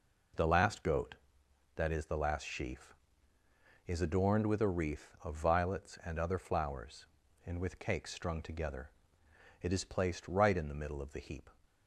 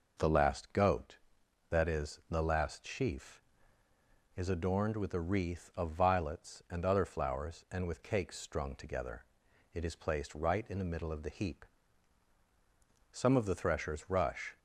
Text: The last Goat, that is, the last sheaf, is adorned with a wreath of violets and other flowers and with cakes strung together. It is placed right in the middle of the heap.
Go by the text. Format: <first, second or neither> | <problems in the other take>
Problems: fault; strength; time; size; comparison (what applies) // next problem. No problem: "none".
first | goes on to say "Some of the threshers rush"; from 13.1 s on; 1.4 s long